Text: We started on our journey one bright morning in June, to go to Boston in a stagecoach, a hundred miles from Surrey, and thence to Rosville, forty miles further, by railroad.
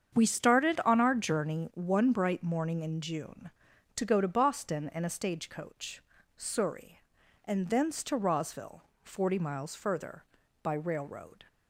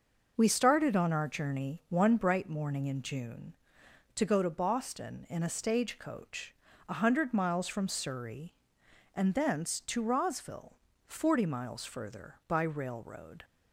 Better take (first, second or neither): second